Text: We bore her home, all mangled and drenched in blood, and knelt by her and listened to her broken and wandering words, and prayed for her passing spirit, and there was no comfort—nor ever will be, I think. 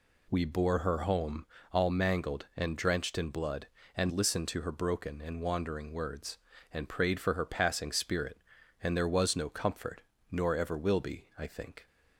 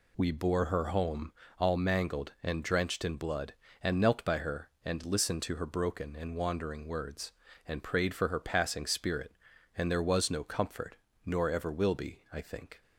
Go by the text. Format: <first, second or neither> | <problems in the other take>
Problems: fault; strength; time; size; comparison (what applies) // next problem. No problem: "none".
second | skips "knelt by her and"; at 4.1 s